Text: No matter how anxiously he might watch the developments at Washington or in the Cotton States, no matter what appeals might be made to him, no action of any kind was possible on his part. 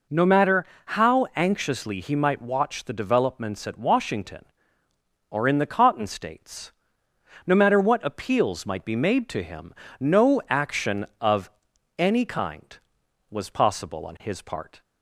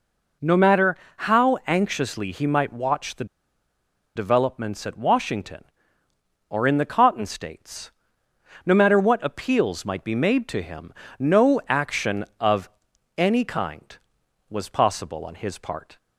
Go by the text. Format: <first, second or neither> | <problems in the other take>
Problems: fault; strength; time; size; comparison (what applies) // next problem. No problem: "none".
first | pauses between "matter" and "how"; slight; at 0.9 s; 0.22 s long; slight in the first // pauses between "the" and "developments"; noticeable; at 3.2 s; 0.90 s long // pauses between "of" and "any"; noticeable; at 12.6 s; 0.48 s long; noticeable in the first